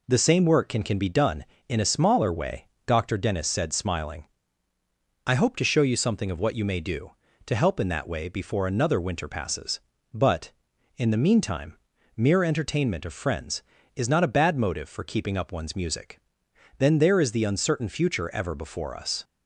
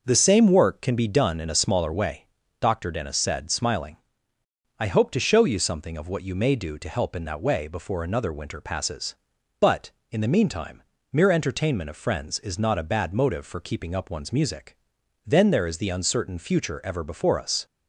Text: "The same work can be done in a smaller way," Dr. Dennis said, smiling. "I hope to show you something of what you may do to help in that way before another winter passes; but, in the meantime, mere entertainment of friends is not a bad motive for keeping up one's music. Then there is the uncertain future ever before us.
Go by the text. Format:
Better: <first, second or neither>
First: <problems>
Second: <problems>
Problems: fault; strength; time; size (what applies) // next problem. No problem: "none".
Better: second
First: says "can" twice; at 0.8 s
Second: none